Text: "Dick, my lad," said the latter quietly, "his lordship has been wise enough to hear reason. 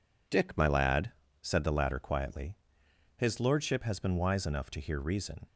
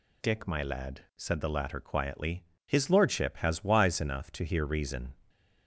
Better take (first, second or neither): first